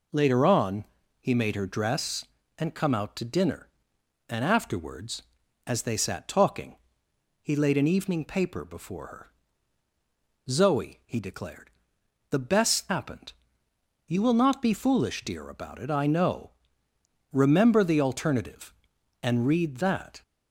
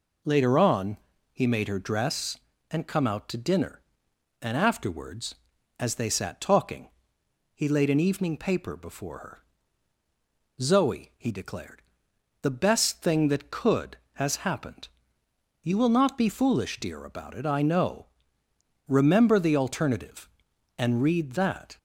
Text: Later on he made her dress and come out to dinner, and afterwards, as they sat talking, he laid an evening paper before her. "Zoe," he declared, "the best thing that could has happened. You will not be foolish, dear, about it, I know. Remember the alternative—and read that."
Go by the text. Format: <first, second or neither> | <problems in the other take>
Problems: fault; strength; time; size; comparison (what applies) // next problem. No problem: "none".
second | pauses between "on" and "he"; slight; at 0.8 s; 0.36 s long; slight in the second // skips "thing that could has"; at 12.9 s